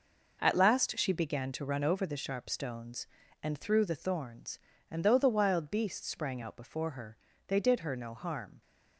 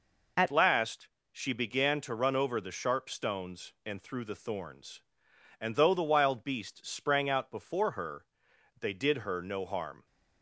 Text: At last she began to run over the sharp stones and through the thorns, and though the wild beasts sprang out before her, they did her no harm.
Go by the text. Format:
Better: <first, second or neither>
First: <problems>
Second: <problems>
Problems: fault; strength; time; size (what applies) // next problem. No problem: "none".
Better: first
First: none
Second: changes voice at "last"; from 0.5 s on; 9.5 s long // pauses between "last" and "she"; slight; at 1.0 s; 0.24 s long